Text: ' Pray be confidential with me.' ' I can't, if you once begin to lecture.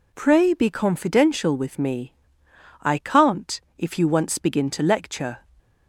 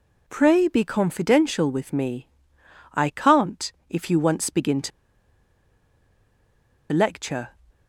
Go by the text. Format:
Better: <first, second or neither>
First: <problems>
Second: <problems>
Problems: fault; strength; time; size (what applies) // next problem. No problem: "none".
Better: first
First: none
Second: pauses between "to" and "lecture"; strong; at 4.9 s; 2.0 s long